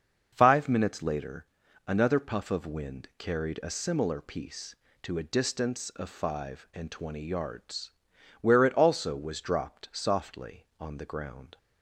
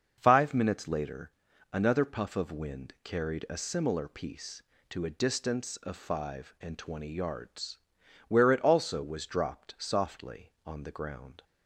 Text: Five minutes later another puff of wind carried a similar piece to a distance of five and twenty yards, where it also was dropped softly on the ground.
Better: neither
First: starts louder than the rest; until 1.3 s; 6.5 dB // pauses between "later" and "another"; at 1.4 s; 0.40 s long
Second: starts louder than the rest; until 1.1 s; 6.5 dB // pauses between "later" and "another"; at 1.3 s; 0.40 s long

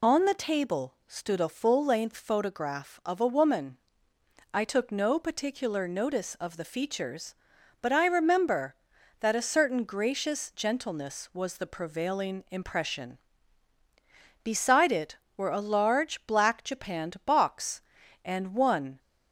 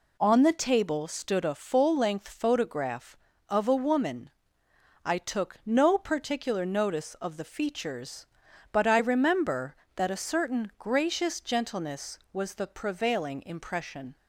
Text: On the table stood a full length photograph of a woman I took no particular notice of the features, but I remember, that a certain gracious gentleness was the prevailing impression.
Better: second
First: pauses between "woman" and "I"; noticeable; at 3.7 s; 0.74 s long // goes on to say "Beside it were a large black japanned box and one"; strong; from 14.4 s on; 4.5 s long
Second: pauses between "woman" and "I"; noticeable; at 4.2 s; 0.78 s long

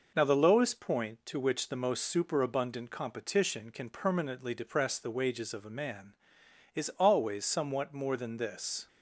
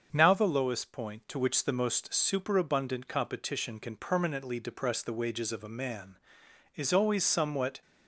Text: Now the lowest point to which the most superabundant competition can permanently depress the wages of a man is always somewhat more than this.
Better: first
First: none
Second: starts louder than the rest; until 1.1 s; 6.5 dB // stops before "more than this"; at 7.8 s

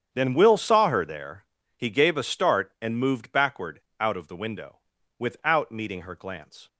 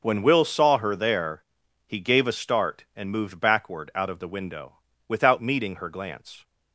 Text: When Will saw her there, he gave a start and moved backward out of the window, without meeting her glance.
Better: second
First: starts louder than the rest; strong; until 1.1 s; 8.5 dB // says "Then" for "When"; at 0.1 s // pauses between "backward" and "out"; slight; at 3.7 s; 0.20 s long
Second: none

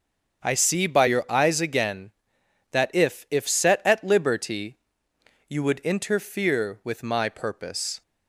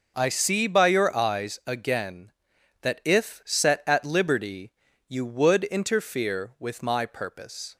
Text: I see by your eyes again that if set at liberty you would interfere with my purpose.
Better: second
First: starts louder than the rest; strong; until 1.5 s; 7.5 dB // says "if" twice; at 3.3 s // pauses between "liberty" and "you"; noticeable; at 4.7 s; 0.72 s long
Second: pauses between "liberty" and "you"; at 4.7 s; 0.38 s long

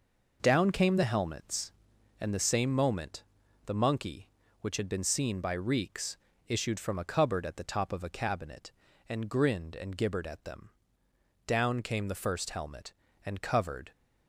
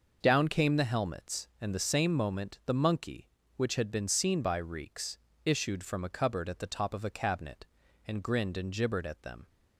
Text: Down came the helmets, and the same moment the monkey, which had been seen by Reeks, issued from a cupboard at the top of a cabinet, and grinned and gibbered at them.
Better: second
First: pauses between "moment" and "the"; at 3.2 s; 0.42 s long // goes on to say "Down came the first helmet and covered"; strong; from 11.4 s on; 2.4 s long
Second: none

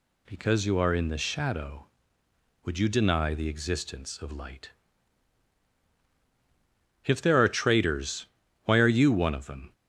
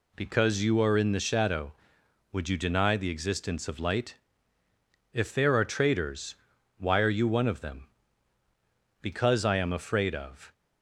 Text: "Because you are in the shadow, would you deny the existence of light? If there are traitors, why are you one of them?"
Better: first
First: none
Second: goes on to say "Because I am afraid of"; from 9.0 s on; 1.5 s long

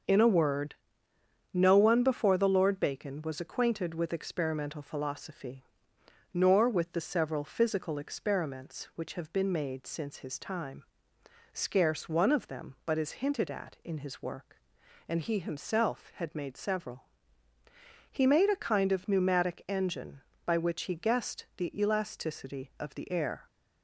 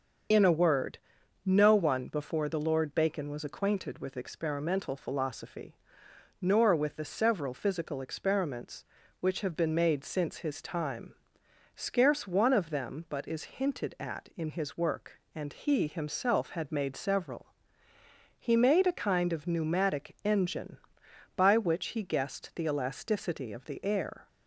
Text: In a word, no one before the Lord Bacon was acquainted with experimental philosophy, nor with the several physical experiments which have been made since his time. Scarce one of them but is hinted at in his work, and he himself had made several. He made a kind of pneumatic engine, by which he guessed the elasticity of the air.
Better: first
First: starts louder than the rest; noticeable; until 1.8 s; 6 dB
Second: loses the start of "In"; at 0.3 s; 45 ms // starts louder than the rest; until 1.7 s; 7 dB

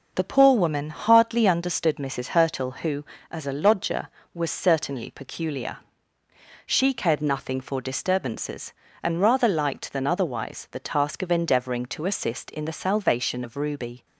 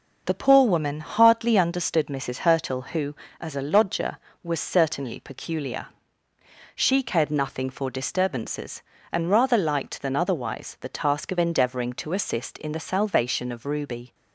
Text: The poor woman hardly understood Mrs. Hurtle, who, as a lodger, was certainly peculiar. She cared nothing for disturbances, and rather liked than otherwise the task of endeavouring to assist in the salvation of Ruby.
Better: neither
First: none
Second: none

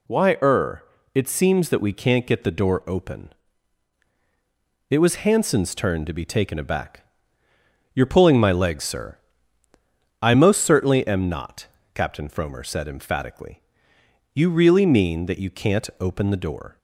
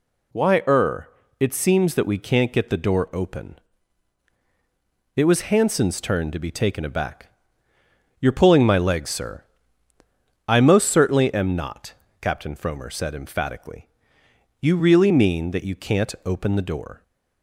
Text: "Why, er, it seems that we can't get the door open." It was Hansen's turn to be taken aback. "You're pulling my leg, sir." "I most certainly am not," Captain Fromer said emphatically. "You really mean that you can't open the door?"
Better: neither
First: none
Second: none

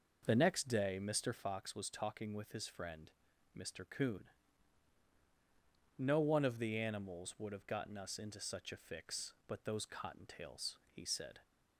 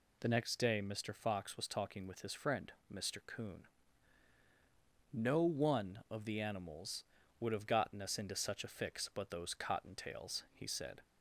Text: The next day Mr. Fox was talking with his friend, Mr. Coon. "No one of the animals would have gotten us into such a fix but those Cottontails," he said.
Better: second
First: starts louder than the rest; noticeable; until 1.4 s; 6 dB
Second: none

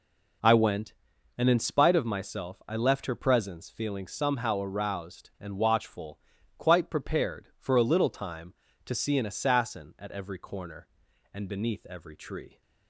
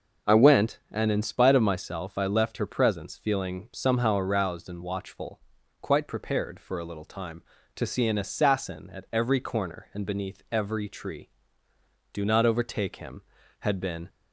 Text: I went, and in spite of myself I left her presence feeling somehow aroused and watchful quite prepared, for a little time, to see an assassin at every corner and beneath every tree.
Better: first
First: pauses between "watchful" and "quite"; at 6.1 s; 0.38 s long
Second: pauses between "watchful" and "quite"; at 5.3 s; 0.42 s long // goes on to say "Do not overtake him had been"; strong; from 12.1 s on; 1.9 s long

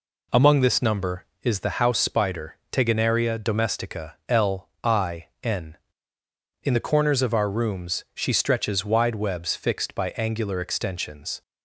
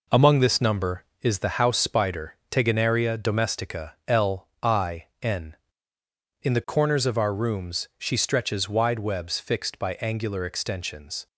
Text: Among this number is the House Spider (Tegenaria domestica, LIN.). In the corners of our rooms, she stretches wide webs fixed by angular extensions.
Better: first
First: none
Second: gets quieter; throughout; 6.5 dB

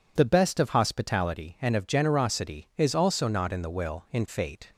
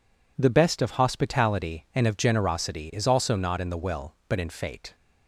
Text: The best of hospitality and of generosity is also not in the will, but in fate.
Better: second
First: skips "but"; at 4.0 s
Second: none

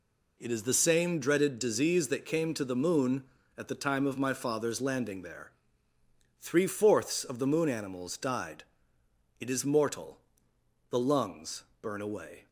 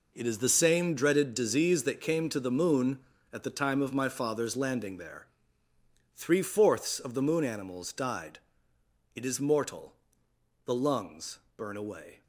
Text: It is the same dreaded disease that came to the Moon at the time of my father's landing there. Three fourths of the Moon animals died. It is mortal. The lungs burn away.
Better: first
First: pauses between "lungs" and "burn"; slight; at 11.6 s; 0.18 s long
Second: gets quieter; strong; throughout; 10.5 dB // pauses between "lungs" and "burn"; slight; at 11.3 s; 0.18 s long

